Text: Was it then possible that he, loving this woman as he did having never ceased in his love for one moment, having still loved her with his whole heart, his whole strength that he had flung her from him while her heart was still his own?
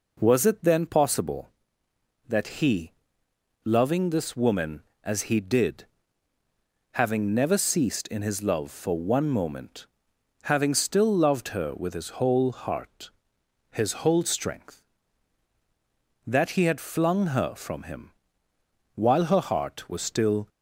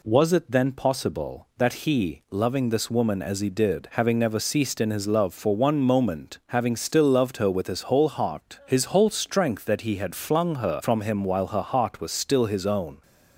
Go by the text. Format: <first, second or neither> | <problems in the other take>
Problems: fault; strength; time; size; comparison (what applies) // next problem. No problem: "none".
second | pauses between "did" and "having"; at 5.8 s; 1.0 s long // pauses between "him" and "while"; noticeable; at 18.1 s; 0.86 s long // stops before "his own"; at 20.4 s